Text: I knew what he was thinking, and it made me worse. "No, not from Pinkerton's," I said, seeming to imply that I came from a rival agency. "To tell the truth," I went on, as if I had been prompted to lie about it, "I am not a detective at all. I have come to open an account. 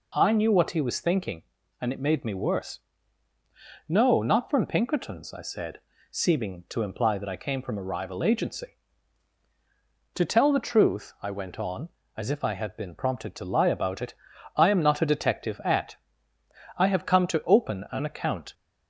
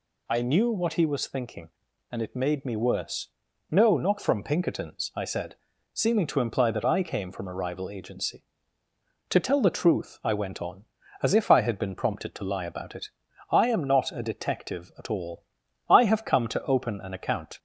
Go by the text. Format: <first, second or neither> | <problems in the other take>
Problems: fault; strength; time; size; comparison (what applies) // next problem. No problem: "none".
second | skips "all"; at 16.3 s